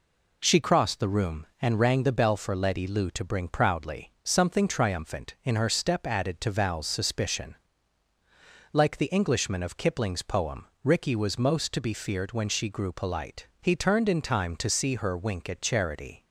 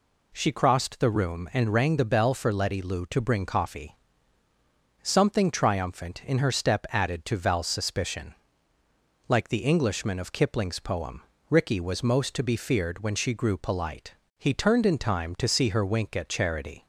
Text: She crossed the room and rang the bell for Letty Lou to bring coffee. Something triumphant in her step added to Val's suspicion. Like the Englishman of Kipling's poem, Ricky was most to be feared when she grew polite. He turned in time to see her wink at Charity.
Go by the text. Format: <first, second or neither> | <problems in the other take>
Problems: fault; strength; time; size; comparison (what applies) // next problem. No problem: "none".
second | says "proudly" for "coffee"; at 3.4 s